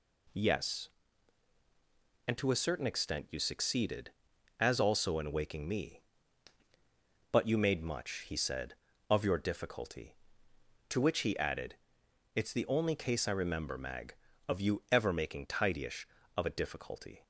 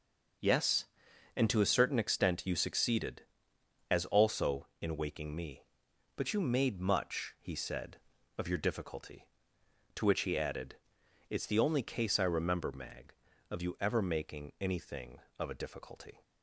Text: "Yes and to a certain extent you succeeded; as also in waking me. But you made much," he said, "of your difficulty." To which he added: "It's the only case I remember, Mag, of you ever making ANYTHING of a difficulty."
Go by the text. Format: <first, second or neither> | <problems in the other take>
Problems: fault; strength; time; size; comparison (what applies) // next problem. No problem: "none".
second | says "Tidyish" for "ANYTHING"; at 15.4 s